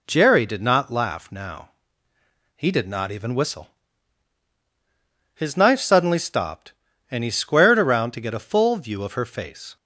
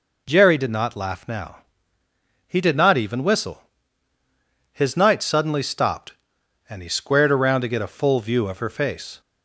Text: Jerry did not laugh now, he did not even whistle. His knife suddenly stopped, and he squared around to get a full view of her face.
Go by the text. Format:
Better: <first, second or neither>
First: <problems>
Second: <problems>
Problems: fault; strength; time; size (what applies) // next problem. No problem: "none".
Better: first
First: none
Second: says "night" for "knife"; at 4.9 s